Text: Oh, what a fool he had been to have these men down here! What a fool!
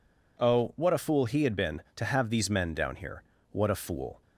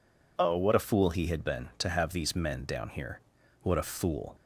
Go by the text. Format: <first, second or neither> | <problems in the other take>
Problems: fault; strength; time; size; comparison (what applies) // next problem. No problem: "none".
neither | none